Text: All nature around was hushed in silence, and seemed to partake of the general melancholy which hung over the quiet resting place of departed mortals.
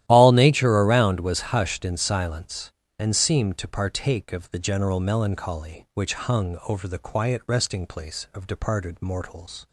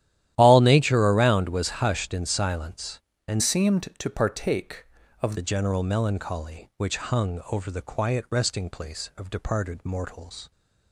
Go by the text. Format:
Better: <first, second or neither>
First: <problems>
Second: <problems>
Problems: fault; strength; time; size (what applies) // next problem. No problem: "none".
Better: first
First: starts louder than the rest; strong; until 1.0 s; 13 dB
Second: starts louder than the rest; strong; until 1.3 s; 12 dB // changes voice from "seemed" to "of"; from 3.4 to 5.3 s; 1.9 s long